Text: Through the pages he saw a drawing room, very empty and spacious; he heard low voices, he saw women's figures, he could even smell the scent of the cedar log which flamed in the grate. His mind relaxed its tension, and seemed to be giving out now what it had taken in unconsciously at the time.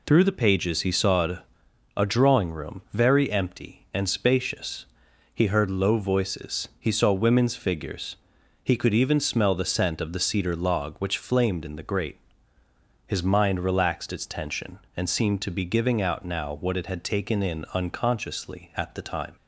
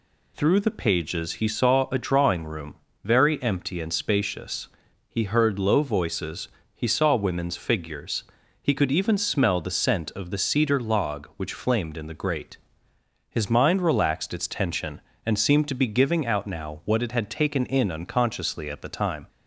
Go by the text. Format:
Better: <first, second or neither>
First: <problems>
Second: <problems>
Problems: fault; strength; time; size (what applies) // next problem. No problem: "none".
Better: second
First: says "a" twice; at 1.9 s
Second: none